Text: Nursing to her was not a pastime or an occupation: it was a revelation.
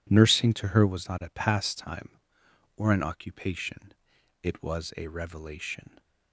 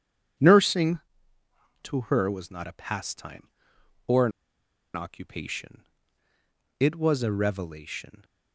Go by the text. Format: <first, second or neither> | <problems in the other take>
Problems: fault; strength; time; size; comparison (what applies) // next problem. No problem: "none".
first | pauses between "an" and "occupation"; noticeable; at 4.3 s; 0.64 s long